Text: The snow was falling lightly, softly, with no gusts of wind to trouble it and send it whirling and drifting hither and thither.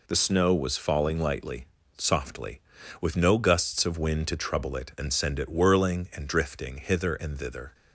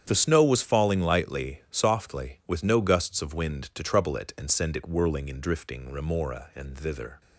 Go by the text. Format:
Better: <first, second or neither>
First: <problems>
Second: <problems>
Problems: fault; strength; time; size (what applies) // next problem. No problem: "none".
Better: first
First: none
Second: starts louder than the rest; strong; until 1.0 s; 8.5 dB // says "remora" for "hither"; at 5.9 s